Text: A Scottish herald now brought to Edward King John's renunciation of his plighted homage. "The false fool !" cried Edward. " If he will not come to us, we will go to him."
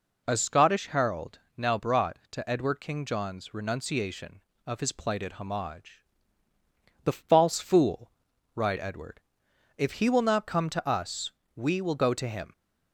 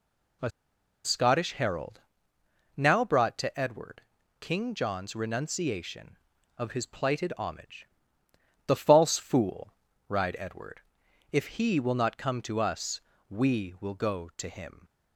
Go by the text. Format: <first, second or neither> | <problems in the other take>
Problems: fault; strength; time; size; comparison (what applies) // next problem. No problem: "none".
first | pauses between "A" and "Scottish"; noticeable; at 0.4 s; 0.55 s long // pauses between "herald" and "now"; noticeable; at 2.0 s; 0.76 s long; slight in the first // pauses between "Edward" and "King"; at 4.0 s; 0.38 s long